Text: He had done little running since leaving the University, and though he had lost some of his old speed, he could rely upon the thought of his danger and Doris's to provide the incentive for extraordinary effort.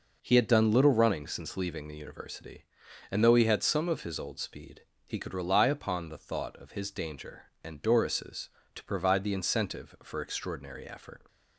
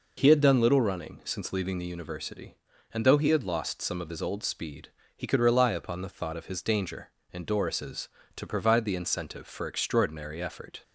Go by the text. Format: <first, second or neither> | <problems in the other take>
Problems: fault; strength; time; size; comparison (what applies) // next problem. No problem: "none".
second | skips "lost"; at 3.6 s